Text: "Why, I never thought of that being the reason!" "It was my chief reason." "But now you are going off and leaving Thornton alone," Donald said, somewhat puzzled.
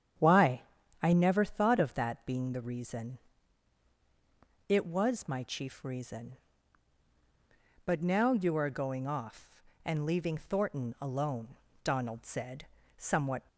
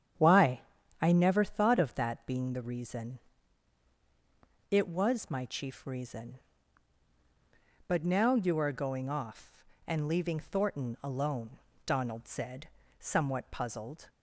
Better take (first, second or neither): second